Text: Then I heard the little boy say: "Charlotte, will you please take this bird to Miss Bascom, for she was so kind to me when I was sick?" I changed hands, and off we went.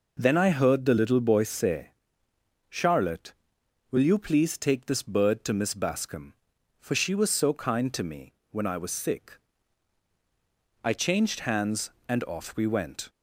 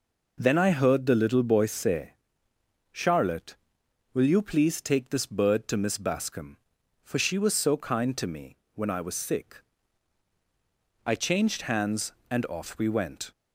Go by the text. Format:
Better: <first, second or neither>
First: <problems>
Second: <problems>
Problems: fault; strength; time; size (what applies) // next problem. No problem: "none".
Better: neither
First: pauses between "me" and "when"; slight; at 8.3 s; 0.18 s long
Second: pauses between "me" and "when"; slight; at 8.5 s; 0.18 s long